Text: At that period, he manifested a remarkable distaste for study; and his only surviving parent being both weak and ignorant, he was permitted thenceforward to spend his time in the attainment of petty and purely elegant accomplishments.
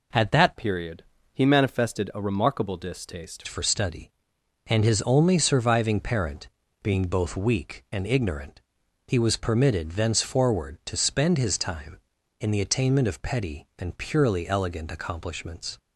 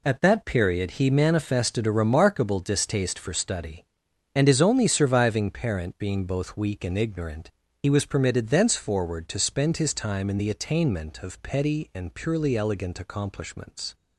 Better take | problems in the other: second | changes voice from "period" to "distaste"; from 0.5 to 3.4 s; 2.9 s long // pauses between "parent" and "being"; slight; at 6.4 s; 0.34 s long

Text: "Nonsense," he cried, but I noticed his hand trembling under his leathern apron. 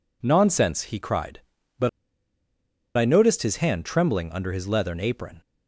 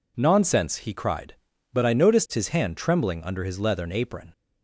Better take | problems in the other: second | pauses between "but" and "I"; at 1.8 s; 1.0 s long

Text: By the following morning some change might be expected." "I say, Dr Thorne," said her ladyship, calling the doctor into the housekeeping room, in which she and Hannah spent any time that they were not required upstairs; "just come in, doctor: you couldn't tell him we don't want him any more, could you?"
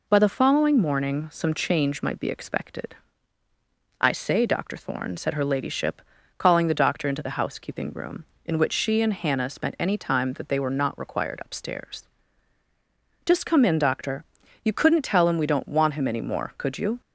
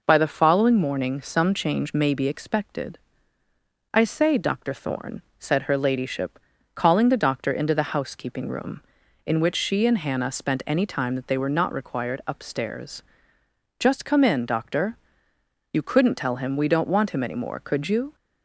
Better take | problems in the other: first | says "may" for "might"; at 1.9 s

